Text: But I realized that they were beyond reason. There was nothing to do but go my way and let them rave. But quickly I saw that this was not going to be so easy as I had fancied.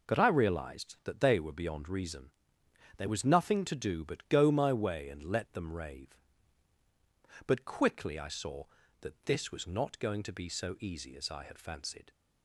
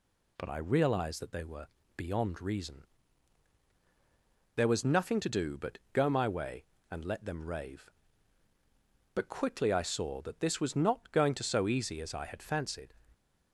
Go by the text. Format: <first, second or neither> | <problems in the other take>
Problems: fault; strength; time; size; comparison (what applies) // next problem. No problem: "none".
first | pauses between "were" and "beyond"; slight; at 1.6 s; 0.28 s long // pauses between "but" and "go"; slight; at 5.7 s; 0.16 s long // skips "be"; at 11.4 s